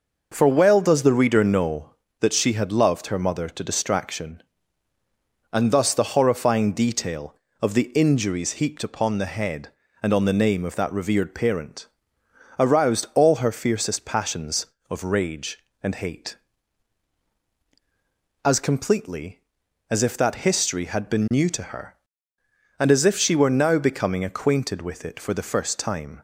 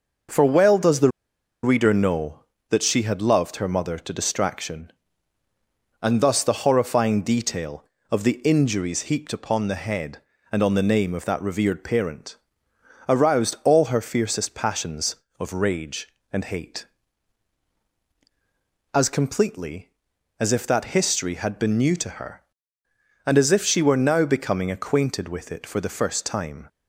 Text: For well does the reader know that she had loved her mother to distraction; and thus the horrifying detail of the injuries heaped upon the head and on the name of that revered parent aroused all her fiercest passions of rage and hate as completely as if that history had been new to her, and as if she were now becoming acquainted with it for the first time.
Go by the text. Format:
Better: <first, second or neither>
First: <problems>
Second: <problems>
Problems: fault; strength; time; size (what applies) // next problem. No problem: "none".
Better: first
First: pauses between "parent" and "aroused"; noticeable; at 11.8 s; 0.72 s long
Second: pauses between "the" and "reader"; noticeable; at 1.0 s; 0.53 s long // pauses between "parent" and "aroused"; noticeable; at 12.3 s; 0.72 s long